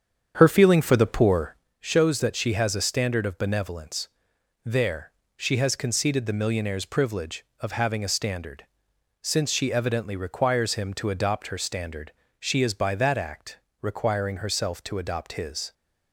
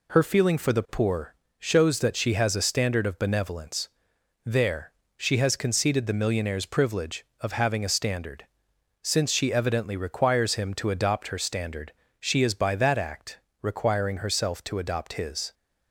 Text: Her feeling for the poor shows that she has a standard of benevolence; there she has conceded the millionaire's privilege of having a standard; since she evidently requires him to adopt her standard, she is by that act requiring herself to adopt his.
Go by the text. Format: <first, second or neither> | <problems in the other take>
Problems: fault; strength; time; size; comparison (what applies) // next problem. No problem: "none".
second | starts louder than the rest; strong; until 1.7 s; 8 dB // pauses between "poor" and "shows"; slight; at 1.5 s; 0.24 s long; slight in the second // pauses between "there" and "she"; slight; at 5.1 s; 0.26 s long; slight in the second // pauses between "act" and "requiring"; slight; at 13.5 s; 0.24 s long; slight in the second